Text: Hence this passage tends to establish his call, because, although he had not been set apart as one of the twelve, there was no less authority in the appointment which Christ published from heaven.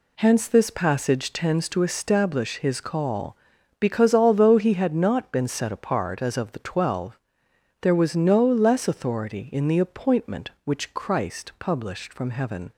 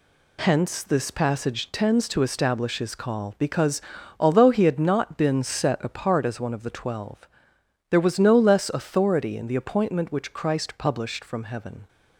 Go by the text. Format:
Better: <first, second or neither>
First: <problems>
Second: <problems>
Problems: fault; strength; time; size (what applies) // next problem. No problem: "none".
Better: second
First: skips "one"; at 6.3 s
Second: none